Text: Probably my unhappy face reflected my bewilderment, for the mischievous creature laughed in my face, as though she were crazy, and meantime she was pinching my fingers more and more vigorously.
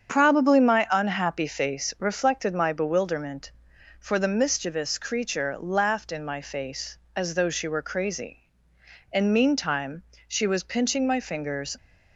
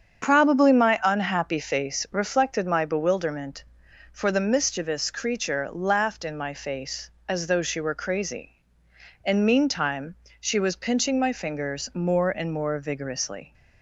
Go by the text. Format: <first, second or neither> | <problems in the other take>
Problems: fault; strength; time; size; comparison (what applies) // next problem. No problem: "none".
second | starts louder than the rest; strong; until 1.1 s; 7.5 dB; strong in the second // pauses between "meantime" and "she"; slight; at 10.0 s; 0.24 s long; slight in the second // stops before "more and more vigorously"; at 11.7 s